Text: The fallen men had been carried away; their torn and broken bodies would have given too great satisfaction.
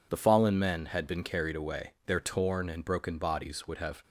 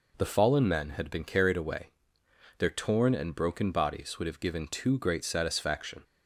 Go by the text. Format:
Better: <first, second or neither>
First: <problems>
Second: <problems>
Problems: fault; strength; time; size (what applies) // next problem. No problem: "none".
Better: second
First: stops before "given too great satisfaction"; at 4.0 s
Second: none